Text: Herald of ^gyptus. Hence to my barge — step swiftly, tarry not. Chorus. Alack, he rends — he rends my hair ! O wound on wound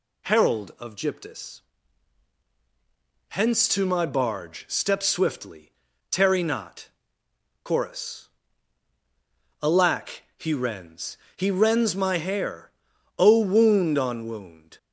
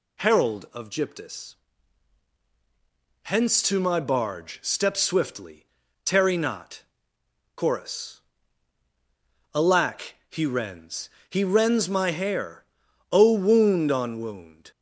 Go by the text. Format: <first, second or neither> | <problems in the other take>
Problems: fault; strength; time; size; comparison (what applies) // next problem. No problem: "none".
neither | none